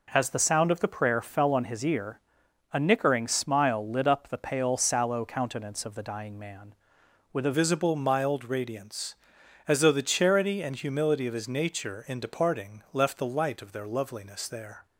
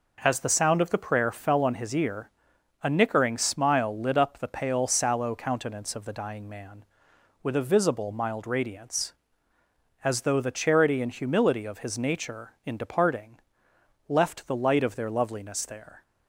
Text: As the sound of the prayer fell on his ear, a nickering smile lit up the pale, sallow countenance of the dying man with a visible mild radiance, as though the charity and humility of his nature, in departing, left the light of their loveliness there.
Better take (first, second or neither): second